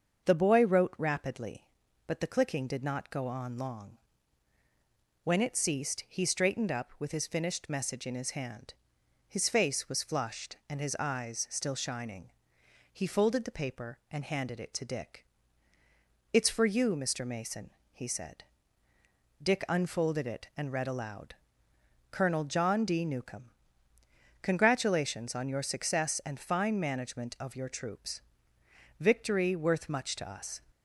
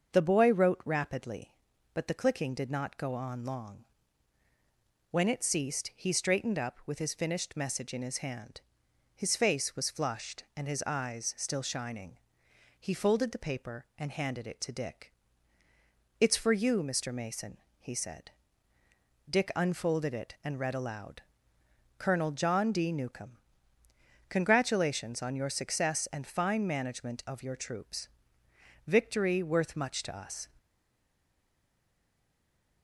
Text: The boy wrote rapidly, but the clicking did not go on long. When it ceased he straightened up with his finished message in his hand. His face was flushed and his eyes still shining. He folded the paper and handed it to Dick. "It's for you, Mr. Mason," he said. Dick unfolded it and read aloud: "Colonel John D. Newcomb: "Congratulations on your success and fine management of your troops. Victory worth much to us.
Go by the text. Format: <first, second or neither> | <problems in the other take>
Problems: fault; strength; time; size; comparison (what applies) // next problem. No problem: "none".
first | starts louder than the rest; until 1.1 s; 6.5 dB; also in the first // stays silent after the last word; from 30.5 s on; 2.3 s long